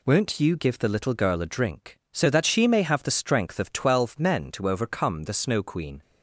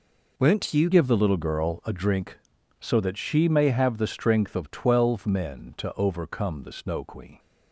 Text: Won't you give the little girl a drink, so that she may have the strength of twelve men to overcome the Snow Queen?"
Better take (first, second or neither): first